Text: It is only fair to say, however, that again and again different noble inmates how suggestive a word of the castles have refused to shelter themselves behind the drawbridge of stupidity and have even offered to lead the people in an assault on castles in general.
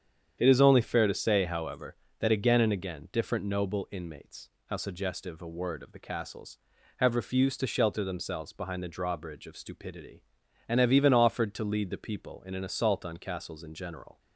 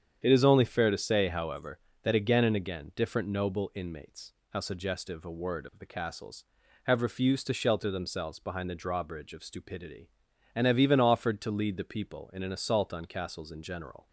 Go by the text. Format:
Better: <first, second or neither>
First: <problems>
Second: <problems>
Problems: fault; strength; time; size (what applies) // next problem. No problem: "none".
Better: neither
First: starts louder than the rest; strong; until 1.3 s; 8.5 dB // pauses between "inmates" and "how"; slight; at 4.4 s; 0.18 s long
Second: starts louder than the rest; strong; until 1.2 s; 8.5 dB // pauses between "inmates" and "how"; slight; at 4.3 s; 0.18 s long